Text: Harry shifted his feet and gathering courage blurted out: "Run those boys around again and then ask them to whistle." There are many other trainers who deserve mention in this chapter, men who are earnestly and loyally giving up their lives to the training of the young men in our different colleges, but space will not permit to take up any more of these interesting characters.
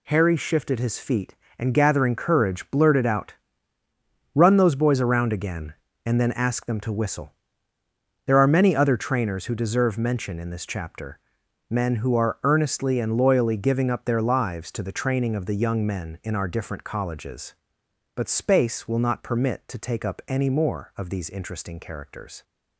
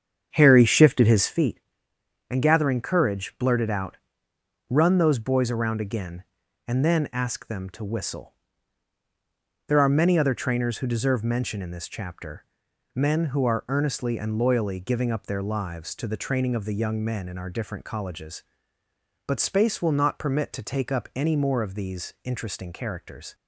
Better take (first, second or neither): first